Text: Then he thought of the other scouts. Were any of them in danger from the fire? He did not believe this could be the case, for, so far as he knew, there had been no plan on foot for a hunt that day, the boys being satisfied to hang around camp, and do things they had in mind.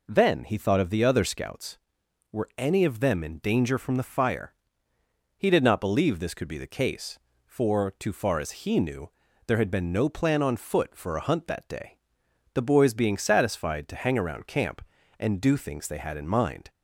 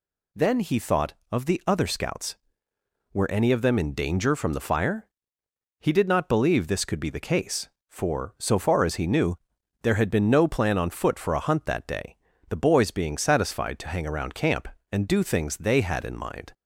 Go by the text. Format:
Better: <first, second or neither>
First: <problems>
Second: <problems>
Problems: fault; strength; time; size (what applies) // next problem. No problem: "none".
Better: second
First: says "too" for "so"; at 7.9 s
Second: none